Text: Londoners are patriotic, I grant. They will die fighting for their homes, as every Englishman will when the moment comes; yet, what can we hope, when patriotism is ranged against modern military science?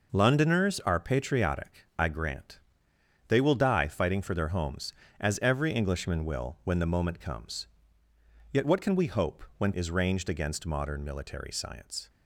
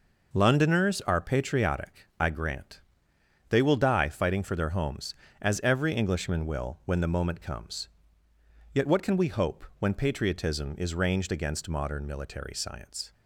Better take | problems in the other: second | skips "patriotism"; at 9.7 s

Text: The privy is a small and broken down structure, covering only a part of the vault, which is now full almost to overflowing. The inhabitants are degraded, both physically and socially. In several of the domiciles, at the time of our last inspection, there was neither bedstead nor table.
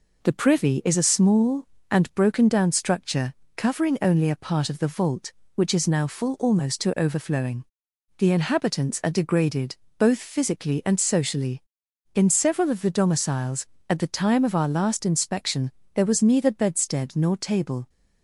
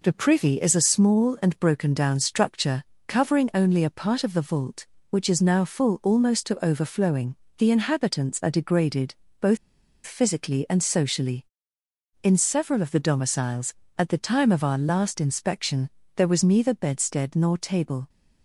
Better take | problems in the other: first | pauses between "both" and "physically"; noticeable; at 9.5 s; 0.49 s long

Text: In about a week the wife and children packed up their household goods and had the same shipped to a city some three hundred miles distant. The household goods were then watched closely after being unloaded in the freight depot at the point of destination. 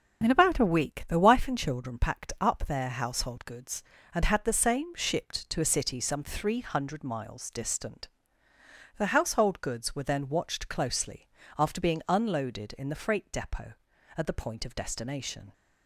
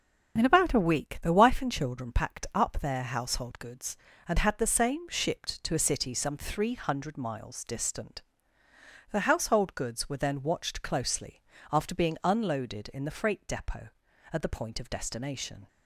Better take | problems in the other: neither | starts louder than the rest; the same in both // pauses between "closely" and "after"; slight; the same in both

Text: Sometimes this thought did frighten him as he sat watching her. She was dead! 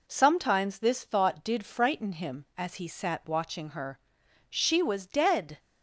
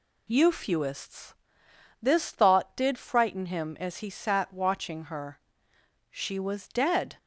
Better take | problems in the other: first | says "Euphuists" for "Sometimes"; at 0.2 s

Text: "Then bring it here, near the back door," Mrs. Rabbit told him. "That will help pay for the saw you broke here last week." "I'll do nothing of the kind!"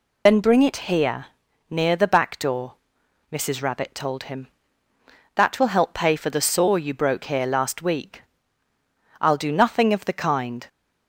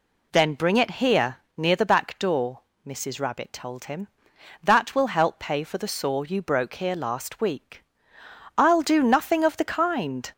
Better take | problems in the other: second | loses the start of "Then"; at 0.2 s; 75 ms

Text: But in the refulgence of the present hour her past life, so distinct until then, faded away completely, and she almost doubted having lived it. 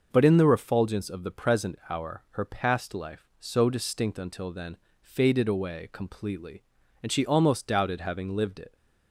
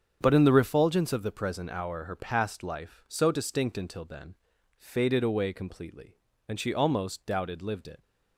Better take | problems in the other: first | starts louder than the rest; strong; until 1.2 s; 7.5 dB; noticeable in the first // skips "having"; at 7.5 s

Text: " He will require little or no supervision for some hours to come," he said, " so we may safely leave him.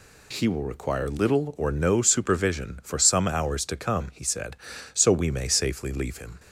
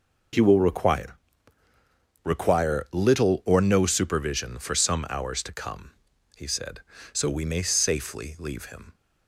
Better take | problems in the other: first | says "require" twice; at 2.2 s

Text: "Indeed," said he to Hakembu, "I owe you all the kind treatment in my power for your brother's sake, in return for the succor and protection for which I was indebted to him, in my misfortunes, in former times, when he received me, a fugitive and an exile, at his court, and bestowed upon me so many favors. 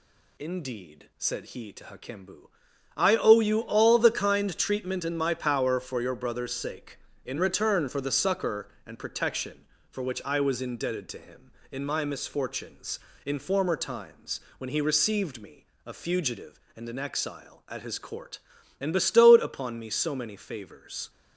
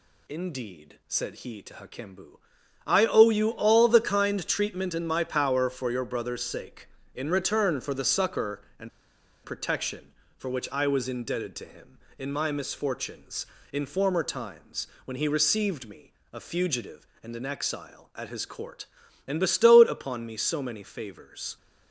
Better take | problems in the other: first | pauses between "and" and "protection"; noticeable; at 8.9 s; 0.54 s long

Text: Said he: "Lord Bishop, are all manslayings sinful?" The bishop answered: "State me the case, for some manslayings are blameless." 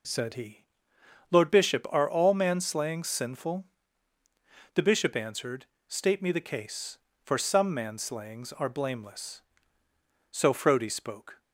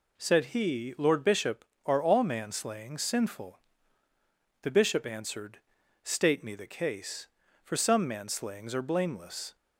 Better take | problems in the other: second | goes on to say "So Frodi spoke"; noticeable; from 10.2 s on; 1.1 s long

